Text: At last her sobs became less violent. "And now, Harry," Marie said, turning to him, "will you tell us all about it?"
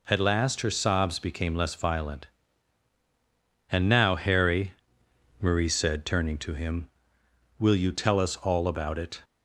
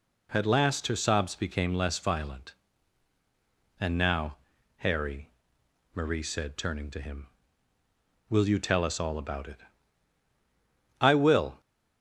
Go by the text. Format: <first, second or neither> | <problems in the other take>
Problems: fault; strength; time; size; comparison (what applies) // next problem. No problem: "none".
first | goes on to say "I will"; from 11.0 s on; 0.60 s long